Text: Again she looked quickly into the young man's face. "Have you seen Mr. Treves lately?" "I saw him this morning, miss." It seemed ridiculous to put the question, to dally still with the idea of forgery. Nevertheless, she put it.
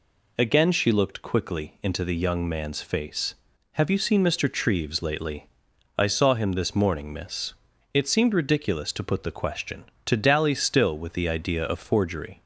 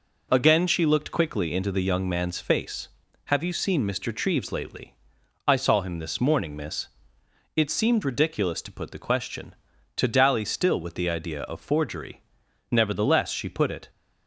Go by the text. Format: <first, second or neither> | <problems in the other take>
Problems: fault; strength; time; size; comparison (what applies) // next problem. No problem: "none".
second | stops before "Nevertheless she put it"; at 12.4 s